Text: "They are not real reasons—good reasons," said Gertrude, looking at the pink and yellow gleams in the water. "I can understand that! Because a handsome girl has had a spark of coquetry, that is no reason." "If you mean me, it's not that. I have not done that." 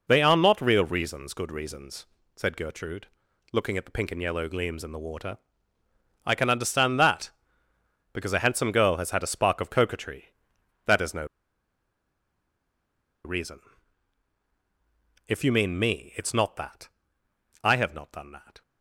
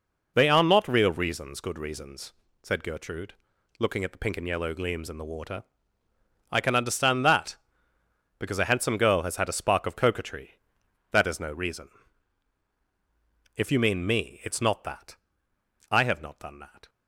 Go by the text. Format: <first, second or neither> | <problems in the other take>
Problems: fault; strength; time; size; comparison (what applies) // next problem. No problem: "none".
second | pauses between "no" and "reason"; strong; at 11.2 s; 1.9 s long